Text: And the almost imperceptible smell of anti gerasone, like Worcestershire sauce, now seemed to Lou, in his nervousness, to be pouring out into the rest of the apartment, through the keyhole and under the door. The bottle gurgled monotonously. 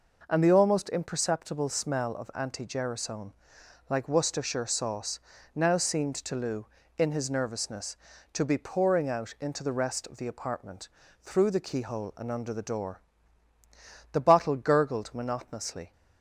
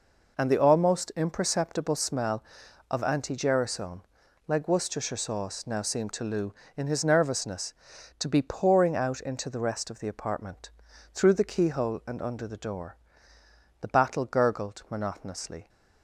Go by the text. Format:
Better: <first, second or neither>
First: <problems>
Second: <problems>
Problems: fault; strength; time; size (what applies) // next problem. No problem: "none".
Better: first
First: none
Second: says "battle" for "bottle"; at 13.8 s